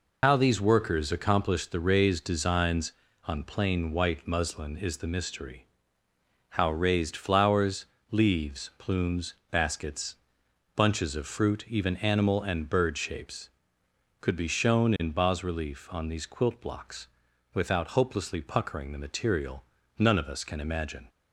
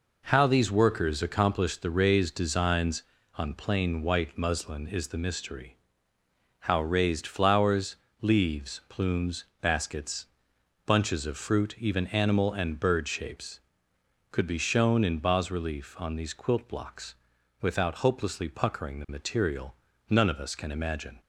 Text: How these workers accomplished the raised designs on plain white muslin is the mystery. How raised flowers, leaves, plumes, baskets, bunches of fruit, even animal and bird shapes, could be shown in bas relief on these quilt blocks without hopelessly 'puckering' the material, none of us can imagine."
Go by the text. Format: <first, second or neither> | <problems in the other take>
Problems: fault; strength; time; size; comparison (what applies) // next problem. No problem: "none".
second | loses the start of "How"; at 0.2 s; 95 ms // pauses between "blocks" and "without"; at 17.0 s; 0.44 s long; also in the second